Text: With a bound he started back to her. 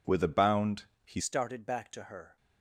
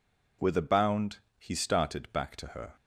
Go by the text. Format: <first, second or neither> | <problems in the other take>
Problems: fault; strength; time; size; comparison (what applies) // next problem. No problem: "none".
second | pauses between "bound" and "he"; slight; at 0.8 s; 0.20 s long; slight in the second // changes voice at "started"; from 1.2 s on; 1.1 s long